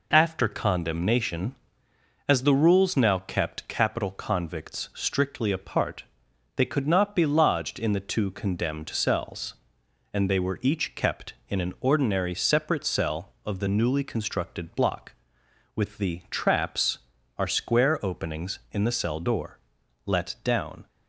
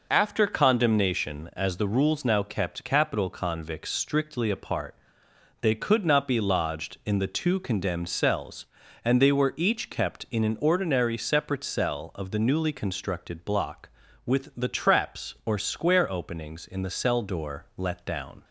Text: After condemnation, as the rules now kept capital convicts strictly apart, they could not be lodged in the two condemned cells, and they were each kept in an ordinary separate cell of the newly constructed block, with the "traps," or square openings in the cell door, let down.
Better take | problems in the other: second | says "are" for "or"; at 17.3 s

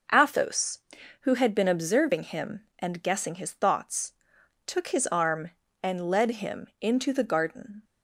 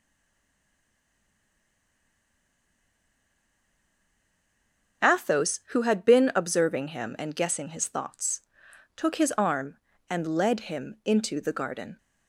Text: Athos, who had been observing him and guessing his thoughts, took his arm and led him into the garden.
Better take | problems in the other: first | stays silent before the first word; strong; until 5.0 s; 5.0 s long // starts louder than the rest; until 6.1 s; 6 dB

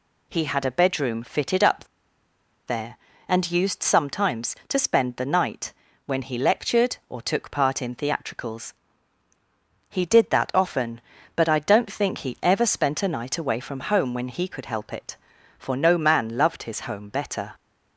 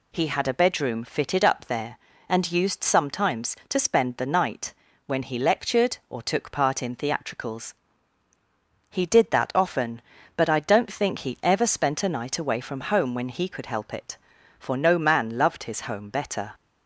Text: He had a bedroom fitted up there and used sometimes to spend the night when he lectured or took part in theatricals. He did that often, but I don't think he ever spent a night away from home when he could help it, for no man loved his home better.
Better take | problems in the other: second | pauses between "up" and "there"; noticeable; at 1.8 s; 0.82 s long // pauses between "night" and "when"; slight; at 5.7 s; 0.32 s long; slight in the second

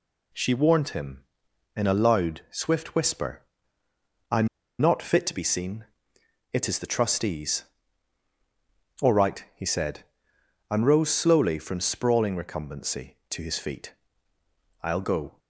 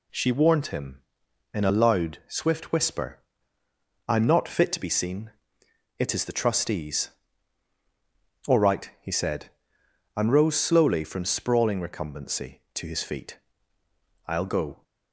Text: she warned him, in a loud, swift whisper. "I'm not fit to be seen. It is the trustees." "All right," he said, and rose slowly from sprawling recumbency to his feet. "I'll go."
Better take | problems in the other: second | pauses between "I'm" and "not"; slight; at 4.4 s; 0.32 s long

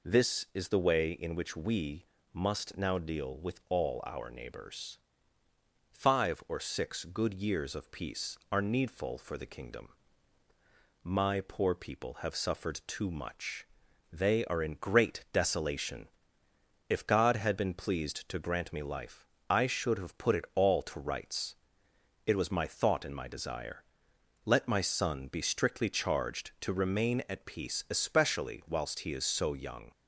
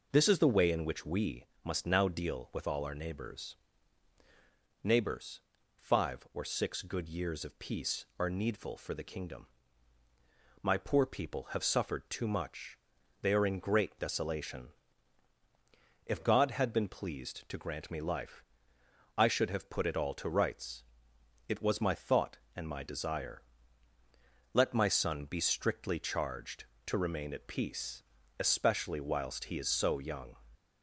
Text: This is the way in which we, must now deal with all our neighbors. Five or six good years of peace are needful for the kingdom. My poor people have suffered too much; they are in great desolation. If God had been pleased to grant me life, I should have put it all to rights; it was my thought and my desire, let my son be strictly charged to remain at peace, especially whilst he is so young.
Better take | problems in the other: first | says "neighbors" twice; at 4.8 s

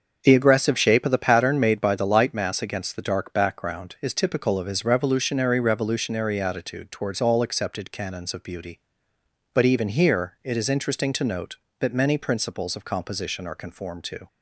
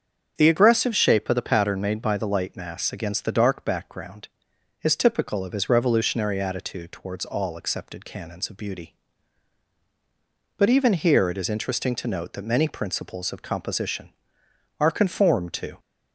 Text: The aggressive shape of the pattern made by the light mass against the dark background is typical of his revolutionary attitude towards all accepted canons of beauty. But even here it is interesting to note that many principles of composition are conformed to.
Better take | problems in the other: second | starts louder than the rest; until 1.2 s; 6.5 dB; strong in the second // says "revolutionary" twice; at 5.5 s

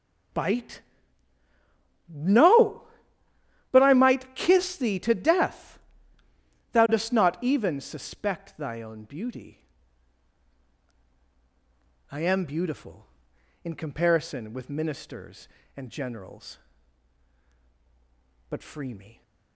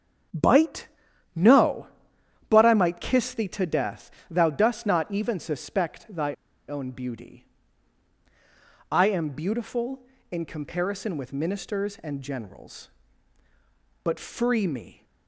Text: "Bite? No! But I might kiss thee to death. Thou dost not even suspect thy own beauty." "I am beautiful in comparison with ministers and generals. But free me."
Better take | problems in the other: first | starts louder than the rest; strong; until 1.7 s; 7.5 dB; strong in the first // pauses between "thy" and "own"; slight; at 6.3 s; 0.34 s long

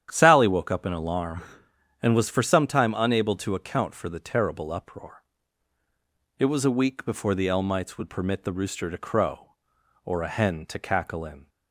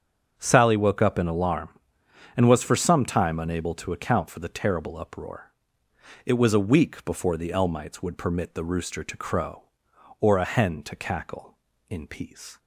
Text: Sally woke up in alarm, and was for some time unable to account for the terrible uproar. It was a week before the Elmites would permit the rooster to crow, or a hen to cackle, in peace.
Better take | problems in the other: second | starts louder than the rest; strong; until 1.1 s; 9.5 dB; also in the second // stops before "peace"; at 11.4 s

